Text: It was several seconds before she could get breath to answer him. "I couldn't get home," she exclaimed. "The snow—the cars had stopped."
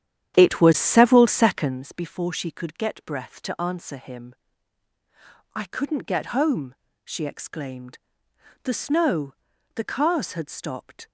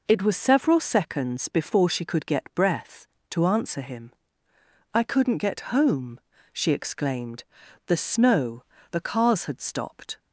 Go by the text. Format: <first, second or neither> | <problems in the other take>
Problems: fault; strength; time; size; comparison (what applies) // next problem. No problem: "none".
second | starts louder than the rest; strong; until 1.9 s; 10 dB